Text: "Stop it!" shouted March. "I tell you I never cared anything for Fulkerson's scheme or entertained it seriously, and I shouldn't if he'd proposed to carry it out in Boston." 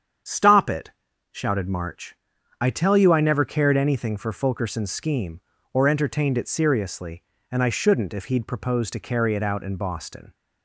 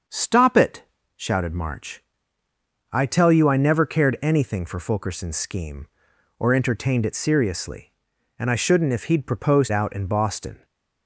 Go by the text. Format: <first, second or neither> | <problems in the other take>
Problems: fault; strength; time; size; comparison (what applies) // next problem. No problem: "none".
first | starts louder than the rest; until 1.4 s; 6.5 dB; strong in the first // skips "to carry it"; at 9.7 s